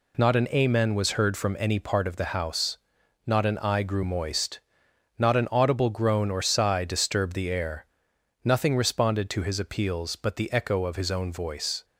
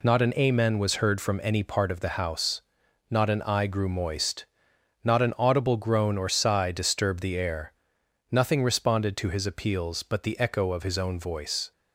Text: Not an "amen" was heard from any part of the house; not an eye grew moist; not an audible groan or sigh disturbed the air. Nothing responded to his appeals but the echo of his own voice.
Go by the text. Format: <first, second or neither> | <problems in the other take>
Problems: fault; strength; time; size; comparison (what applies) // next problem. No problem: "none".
neither | none